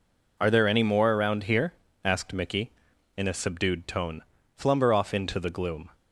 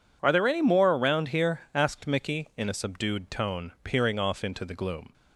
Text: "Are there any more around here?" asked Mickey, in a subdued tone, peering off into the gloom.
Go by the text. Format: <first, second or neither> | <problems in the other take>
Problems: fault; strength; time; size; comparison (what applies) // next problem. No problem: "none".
second | says "flumber" for "peering"; at 4.5 s